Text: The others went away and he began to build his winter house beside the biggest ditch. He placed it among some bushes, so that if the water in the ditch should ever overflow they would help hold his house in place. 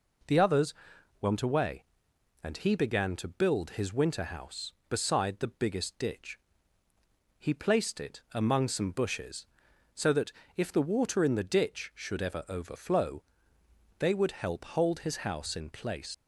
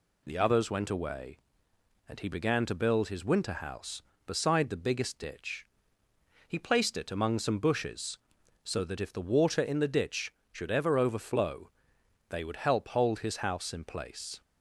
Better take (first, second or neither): second